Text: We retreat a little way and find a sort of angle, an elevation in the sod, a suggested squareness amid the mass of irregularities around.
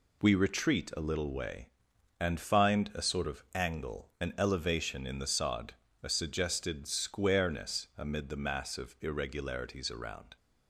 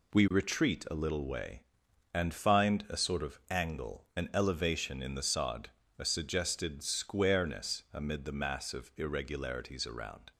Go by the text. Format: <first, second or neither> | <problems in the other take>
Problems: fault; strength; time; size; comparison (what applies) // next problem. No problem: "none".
neither | none